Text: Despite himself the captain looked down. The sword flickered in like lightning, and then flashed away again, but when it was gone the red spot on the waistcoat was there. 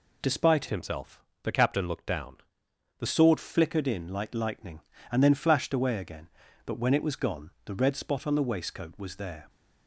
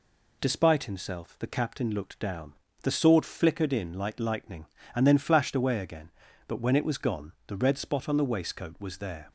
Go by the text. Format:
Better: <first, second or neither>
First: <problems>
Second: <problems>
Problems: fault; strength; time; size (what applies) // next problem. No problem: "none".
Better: second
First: changes voice from "himself" to "The"; from 0.6 to 3.0 s; 2.4 s long // pauses between "himself" and "the"; slight; at 1.2 s; 0.20 s long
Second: none